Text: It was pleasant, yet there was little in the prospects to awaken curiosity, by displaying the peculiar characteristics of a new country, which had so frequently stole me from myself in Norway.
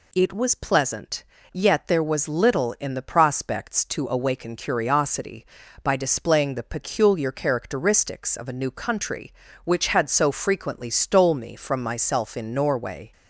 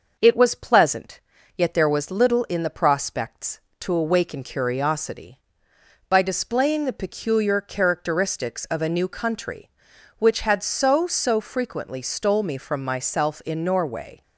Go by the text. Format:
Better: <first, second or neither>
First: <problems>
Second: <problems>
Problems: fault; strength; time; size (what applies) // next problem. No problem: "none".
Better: first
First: none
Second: says "so" twice; at 11.0 s